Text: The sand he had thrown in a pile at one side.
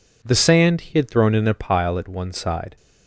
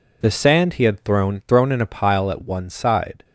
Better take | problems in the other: first | says "thrown" twice; at 1.4 s

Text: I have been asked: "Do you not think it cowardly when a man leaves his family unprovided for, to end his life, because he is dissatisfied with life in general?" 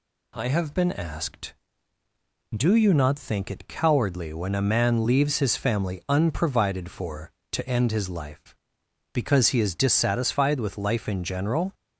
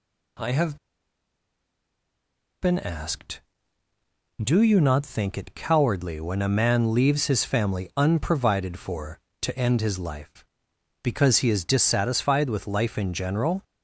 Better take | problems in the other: first | pauses between "have" and "been"; strong; at 0.7 s; 1.8 s long

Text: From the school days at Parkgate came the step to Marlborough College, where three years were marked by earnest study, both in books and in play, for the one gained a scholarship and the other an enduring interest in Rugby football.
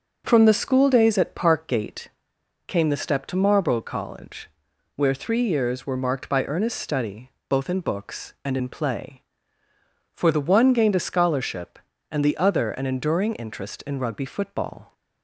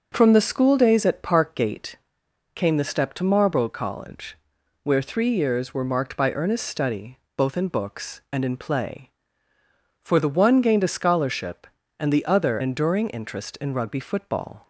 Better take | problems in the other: first | starts louder than the rest; until 1.1 s; 6.5 dB; also in the first // pauses between "Parkgate" and "came"; noticeable; at 1.9 s; 0.58 s long; noticeable in the first // skips "an"; at 12.6 s

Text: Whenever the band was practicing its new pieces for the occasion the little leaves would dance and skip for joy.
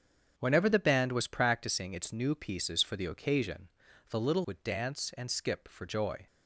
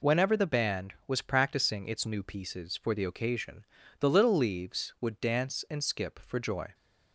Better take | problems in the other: second | starts louder than the rest; strong; until 1.3 s; 7.5 dB // pauses between "occasion" and "the"; at 3.6 s; 0.42 s long; also in the second // skips "leaves"; at 4.4 s

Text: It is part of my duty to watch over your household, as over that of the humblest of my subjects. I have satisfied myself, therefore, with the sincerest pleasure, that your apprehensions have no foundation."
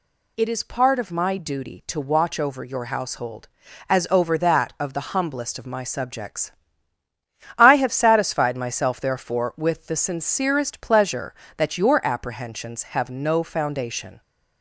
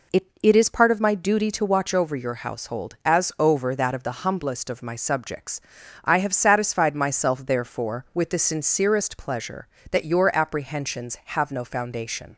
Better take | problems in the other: first | says "It" twice; at 0.4 s

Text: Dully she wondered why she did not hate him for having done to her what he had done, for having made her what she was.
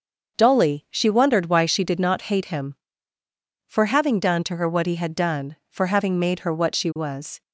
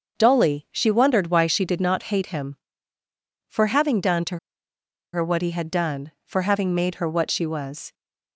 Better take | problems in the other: first | starts louder than the rest; until 1.2 s; 6.5 dB; also in the first // pauses between "to" and "her"; noticeable; at 4.3 s; 0.76 s long

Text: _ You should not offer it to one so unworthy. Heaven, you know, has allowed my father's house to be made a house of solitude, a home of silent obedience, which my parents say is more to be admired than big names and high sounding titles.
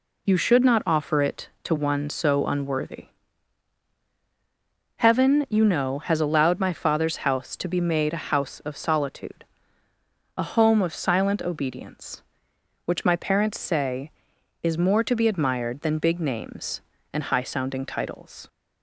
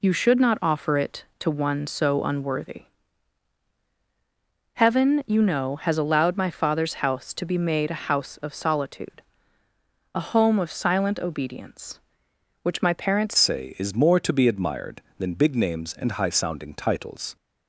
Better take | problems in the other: first | changes voice at "say"; from 13.3 s on; 4.0 s long

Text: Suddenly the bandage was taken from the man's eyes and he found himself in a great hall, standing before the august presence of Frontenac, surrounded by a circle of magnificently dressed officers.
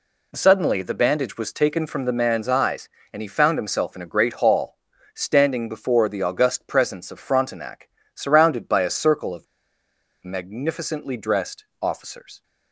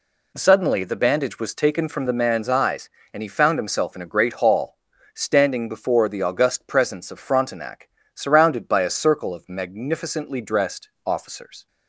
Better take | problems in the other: second | pauses between "of" and "magnificently"; noticeable; at 9.4 s; 0.78 s long // pauses between "dressed" and "officers"; slight; at 11.6 s; 0.16 s long; slight in the second

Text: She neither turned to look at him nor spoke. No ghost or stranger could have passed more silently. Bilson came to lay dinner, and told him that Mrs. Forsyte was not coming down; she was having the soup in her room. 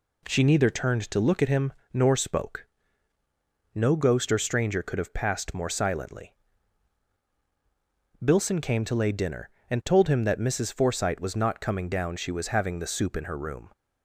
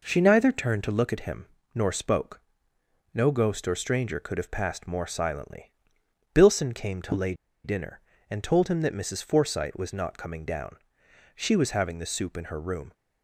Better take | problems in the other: first | pauses between "him" and "nor"; slight; at 1.4 s; 0.28 s long; slight in the first // pauses between "lay" and "dinner"; slight; at 7.3 s; 0.30 s long

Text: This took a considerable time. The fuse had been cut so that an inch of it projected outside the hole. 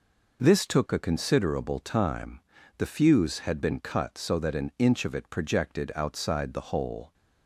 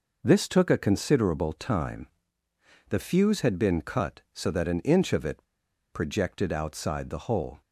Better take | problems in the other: first | pauses between "it" and "projected"; noticeable; at 5.4 s; 0.51 s long

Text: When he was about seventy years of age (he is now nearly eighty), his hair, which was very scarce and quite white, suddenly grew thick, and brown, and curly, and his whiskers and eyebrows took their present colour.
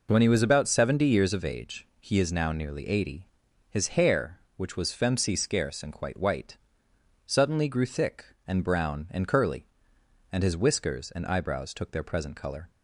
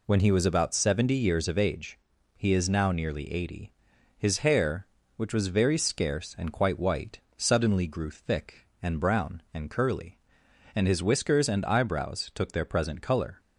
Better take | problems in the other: second | says "femcy" for "very"; at 4.8 s

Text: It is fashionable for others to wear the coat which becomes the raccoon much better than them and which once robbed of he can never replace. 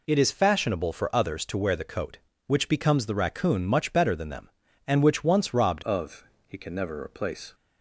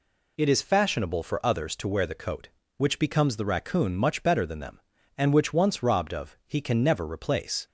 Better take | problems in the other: second | changes voice at "of"; from 5.8 s on; 1.7 s long // pauses between "of" and "he"; slight; at 6.2 s; 0.22 s long

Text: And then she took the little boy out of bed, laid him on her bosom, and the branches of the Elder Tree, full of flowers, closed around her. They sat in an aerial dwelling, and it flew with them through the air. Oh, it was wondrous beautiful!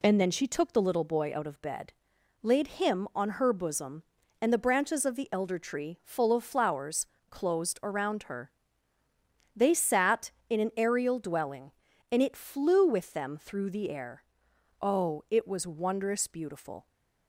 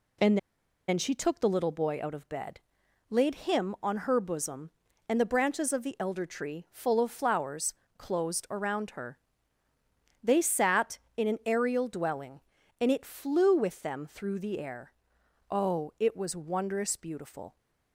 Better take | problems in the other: first | pauses between "And" and "then"; noticeable; at 0.3 s; 0.50 s long

